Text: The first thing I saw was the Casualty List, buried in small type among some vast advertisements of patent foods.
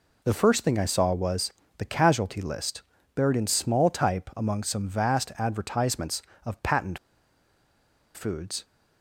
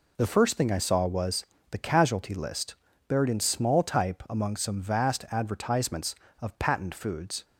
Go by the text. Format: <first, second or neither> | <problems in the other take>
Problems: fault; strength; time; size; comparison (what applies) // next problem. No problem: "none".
second | pauses between "was" and "the"; slight; at 1.5 s; 0.28 s long; slight in the second // pauses between "patent" and "foods"; at 6.9 s; 1.1 s long